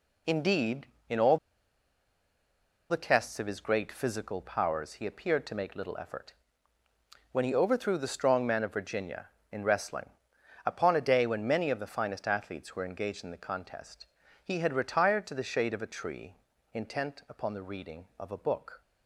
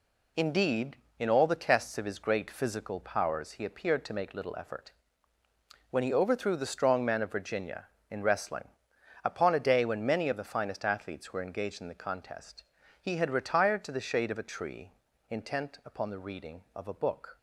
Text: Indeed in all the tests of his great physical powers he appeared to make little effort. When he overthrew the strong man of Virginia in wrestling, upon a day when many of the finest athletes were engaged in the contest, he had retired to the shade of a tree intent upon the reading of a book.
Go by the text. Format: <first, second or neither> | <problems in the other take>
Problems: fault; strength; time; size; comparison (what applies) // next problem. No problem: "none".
second | pauses between "all" and "the"; strong; at 1.3 s; 1.5 s long // pauses between "tree" and "intent"; at 16.3 s; 0.38 s long; also in the second